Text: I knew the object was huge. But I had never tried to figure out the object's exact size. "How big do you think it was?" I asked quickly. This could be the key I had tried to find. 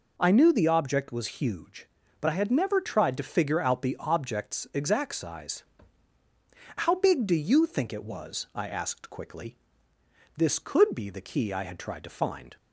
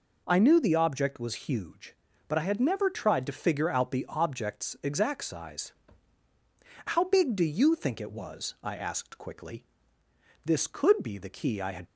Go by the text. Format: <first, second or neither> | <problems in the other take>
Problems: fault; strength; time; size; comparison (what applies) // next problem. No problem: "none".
first | stops before "tried to find"; at 11.8 s